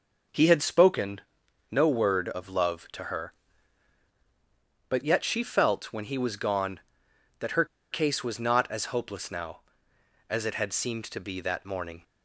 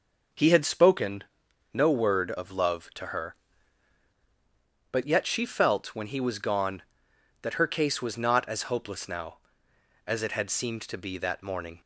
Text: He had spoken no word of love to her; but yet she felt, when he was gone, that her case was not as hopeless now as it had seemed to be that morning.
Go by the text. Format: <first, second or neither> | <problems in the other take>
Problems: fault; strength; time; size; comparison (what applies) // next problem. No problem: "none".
second | pauses between "spoken" and "no"; noticeable; at 1.2 s; 0.50 s long; noticeable in the second // pauses between "her" and "case"; slight; at 7.6 s; 0.26 s long